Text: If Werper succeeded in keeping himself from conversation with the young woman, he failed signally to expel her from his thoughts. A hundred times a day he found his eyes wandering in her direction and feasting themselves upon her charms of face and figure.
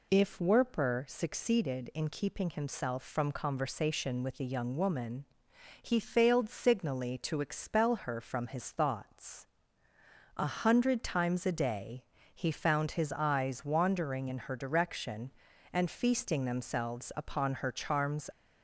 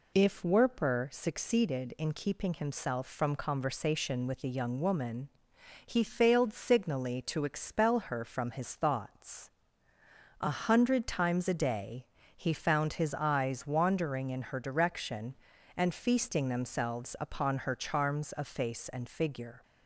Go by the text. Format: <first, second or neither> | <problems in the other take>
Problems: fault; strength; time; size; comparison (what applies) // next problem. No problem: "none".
second | pauses between "day" and "he"; slight; at 12.0 s; 0.28 s long; slight in the second // stops before "of face and figure"; at 18.3 s